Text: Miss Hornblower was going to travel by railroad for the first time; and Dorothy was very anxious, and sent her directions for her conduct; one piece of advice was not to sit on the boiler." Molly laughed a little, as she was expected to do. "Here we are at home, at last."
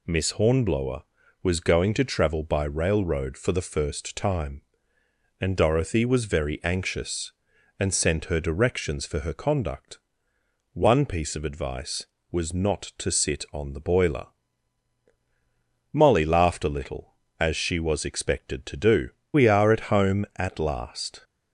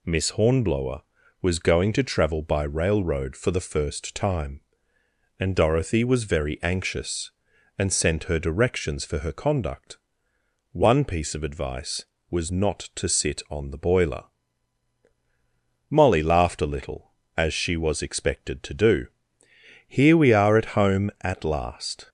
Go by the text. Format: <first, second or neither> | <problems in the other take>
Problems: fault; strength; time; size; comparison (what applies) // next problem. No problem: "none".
second | skips "Here"; at 19.2 s